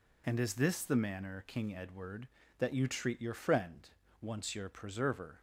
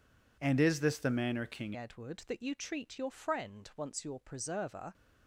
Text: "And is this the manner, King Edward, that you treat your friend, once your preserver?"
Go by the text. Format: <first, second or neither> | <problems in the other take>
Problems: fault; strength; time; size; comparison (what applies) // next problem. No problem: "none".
first | changes voice at "Edward"; from 1.7 s on; 3.2 s long